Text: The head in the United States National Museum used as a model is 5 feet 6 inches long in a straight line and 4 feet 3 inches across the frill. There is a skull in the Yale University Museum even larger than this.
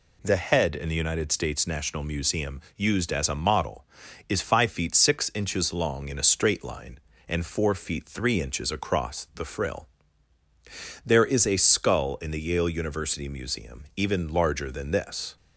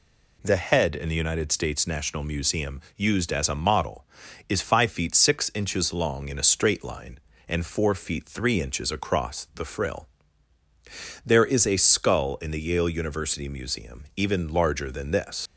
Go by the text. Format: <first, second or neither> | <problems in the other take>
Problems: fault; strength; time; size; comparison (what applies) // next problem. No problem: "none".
first | pauses between "Museum" and "used"; slight; at 2.7 s; 0.16 s long; slight in the first // leaves "this" unfinished; at 15.4 s; 100 ms